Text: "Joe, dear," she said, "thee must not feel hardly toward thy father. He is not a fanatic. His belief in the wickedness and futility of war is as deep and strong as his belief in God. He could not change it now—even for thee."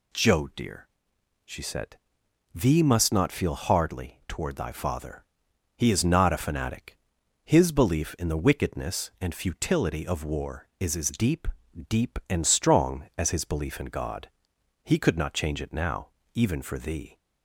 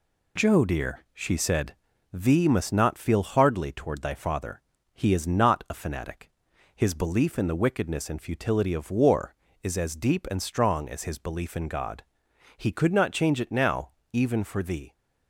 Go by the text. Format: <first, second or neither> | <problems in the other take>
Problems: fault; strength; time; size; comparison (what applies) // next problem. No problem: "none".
second | says "deep" twice; at 11.8 s